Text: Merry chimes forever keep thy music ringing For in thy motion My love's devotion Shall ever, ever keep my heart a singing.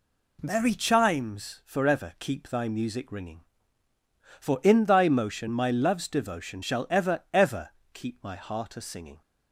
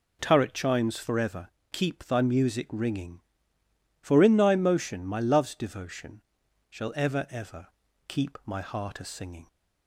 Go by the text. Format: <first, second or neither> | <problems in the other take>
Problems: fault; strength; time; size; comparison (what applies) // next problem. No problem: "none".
first | says "Turret" for "Merry"; at 0.2 s // pauses between "forever" and "keep"; slight; at 1.4 s; 0.24 s long // pauses between "devotion" and "Shall"; noticeable; at 6.2 s; 0.48 s long // pauses between "ever" and "keep"; at 7.6 s; 0.42 s long; slight in the first